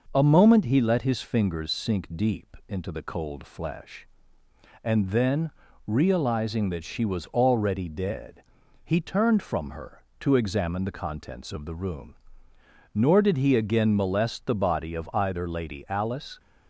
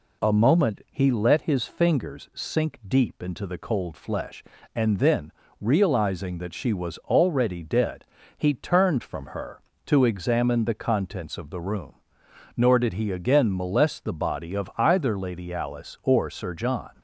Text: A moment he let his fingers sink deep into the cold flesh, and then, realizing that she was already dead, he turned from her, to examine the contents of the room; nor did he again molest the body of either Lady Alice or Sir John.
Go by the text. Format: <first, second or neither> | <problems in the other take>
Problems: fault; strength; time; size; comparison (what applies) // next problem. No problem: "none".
second | stops before "or Sir John"; at 16.3 s